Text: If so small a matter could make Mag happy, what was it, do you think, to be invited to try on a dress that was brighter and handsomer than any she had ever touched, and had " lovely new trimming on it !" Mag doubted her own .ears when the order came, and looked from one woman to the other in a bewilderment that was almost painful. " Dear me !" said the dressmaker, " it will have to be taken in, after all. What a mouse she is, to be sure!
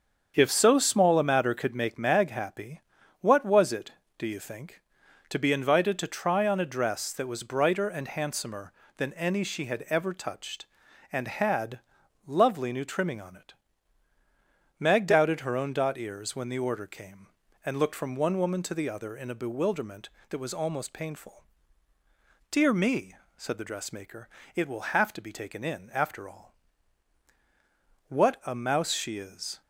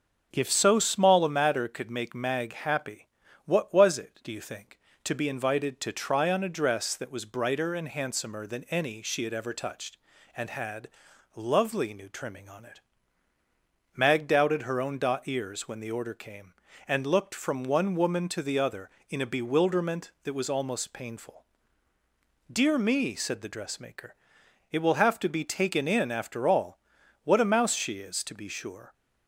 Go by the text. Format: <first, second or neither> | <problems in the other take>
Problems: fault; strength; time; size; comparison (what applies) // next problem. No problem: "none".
second | starts louder than the rest; strong; until 1.3 s; 7 dB; also in the second // stops before "to be sure"; at 29.6 s